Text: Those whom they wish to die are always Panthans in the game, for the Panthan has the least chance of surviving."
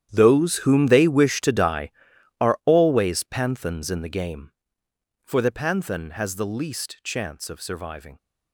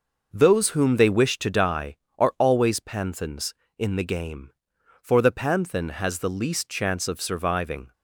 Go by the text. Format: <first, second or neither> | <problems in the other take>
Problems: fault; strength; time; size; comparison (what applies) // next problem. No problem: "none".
second | gets quieter; strong; throughout; 16 dB